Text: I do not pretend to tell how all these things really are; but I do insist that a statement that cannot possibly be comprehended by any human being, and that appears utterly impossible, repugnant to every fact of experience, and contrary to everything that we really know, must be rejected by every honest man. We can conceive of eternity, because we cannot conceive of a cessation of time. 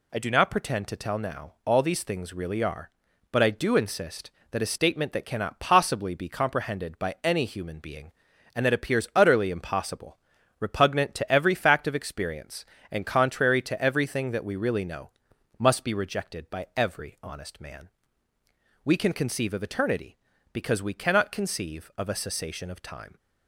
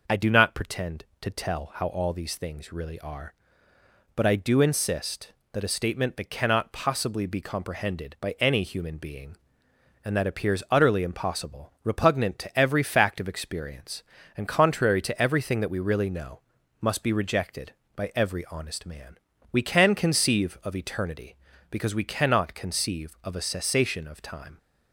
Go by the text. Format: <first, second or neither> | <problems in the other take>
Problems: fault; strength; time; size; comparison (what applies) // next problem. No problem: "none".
second | says "now" for "how"; at 1.1 s